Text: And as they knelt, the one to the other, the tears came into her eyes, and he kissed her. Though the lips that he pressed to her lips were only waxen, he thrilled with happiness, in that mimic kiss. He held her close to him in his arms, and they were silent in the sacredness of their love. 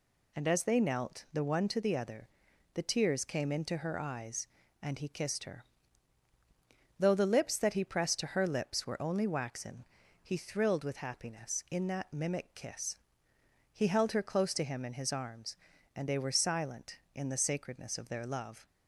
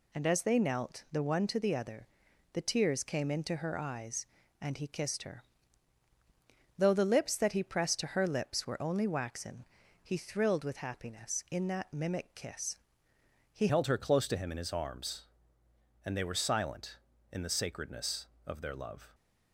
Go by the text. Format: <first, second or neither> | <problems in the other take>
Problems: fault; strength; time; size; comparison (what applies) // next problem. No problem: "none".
first | changes voice at "held"; from 13.6 s on; 5.5 s long